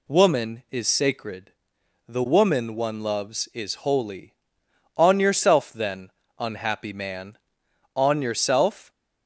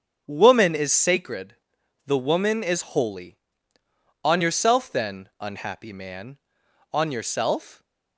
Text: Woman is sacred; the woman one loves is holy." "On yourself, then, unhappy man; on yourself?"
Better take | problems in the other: first | starts louder than the rest; until 1.2 s; 7 dB // skips "one loves"; at 2.6 s

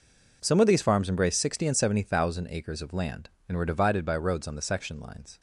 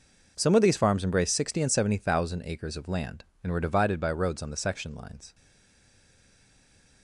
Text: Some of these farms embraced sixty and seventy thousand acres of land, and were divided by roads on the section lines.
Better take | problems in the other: first | stays silent after the last word; noticeable; from 5.3 s on; 1.7 s long

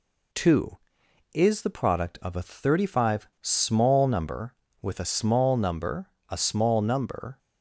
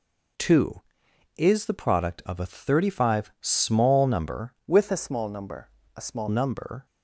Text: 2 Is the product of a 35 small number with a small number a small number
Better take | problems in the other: first | changes voice from "with" to "small"; from 4.6 to 6.2 s; 1.6 s long // pauses between "number" and "a"; slight; at 5.6 s; 0.28 s long; slight in the first

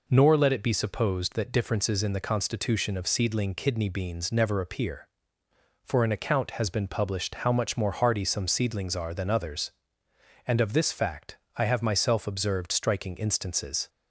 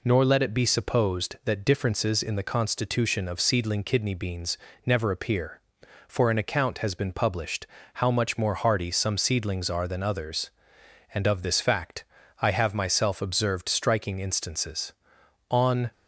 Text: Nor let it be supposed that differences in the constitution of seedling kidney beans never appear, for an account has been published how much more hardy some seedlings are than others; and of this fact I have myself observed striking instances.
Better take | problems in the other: first | pauses between "beans" and "never"; slight; at 4.5 s; 0.30 s long // pauses between "published" and "how"; slight; at 7.6 s; 0.28 s long // pauses between "fact" and "I"; slight; at 12.0 s; 0.36 s long; slight in the first // goes on to say "On"; slight; from 15.5 s on; 0.40 s long

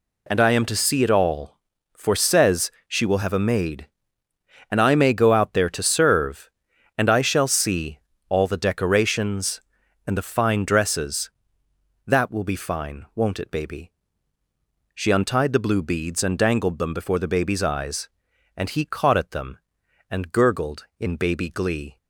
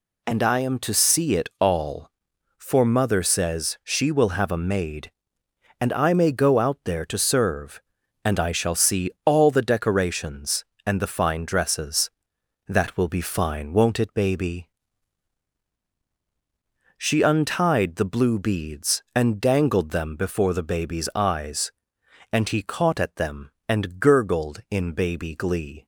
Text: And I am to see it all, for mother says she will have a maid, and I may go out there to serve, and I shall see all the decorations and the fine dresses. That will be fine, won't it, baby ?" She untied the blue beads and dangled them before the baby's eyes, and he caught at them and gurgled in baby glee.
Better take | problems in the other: second | skips "mother"; at 2.1 s // pauses between "says" and "she"; slight; at 2.6 s; 0.18 s long // pauses between "see" and "all"; slight; at 7.9 s; 0.28 s long

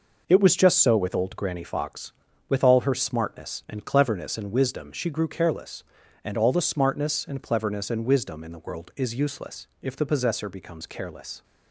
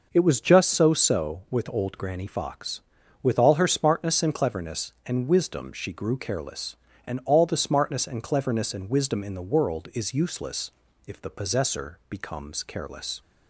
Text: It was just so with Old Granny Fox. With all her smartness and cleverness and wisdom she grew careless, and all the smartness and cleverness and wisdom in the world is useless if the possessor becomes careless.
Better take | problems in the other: first | says "so" twice; at 0.9 s // pauses between "useless" and "if"; slight; at 10.7 s; 0.36 s long; slight in the first

